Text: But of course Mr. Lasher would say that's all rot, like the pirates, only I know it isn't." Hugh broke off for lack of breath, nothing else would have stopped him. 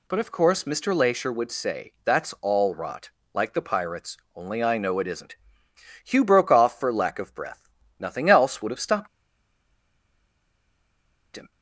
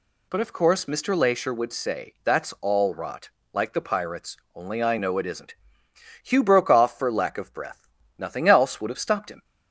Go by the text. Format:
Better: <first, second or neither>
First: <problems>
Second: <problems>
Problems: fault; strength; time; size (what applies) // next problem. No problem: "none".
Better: second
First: pauses between "stopped" and "him"; strong; at 9.0 s; 2.2 s long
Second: none